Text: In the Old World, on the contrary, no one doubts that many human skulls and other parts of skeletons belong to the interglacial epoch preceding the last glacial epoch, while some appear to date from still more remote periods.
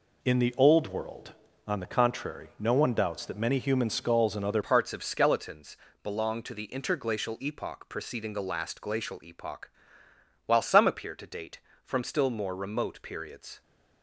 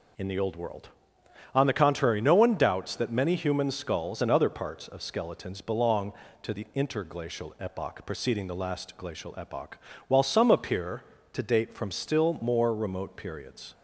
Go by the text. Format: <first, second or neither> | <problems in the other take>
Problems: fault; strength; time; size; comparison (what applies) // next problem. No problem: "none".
second | changes voice at "parts"; from 4.6 s on; 9.0 s long // pauses between "skeletons" and "belong"; slight; at 5.7 s; 0.26 s long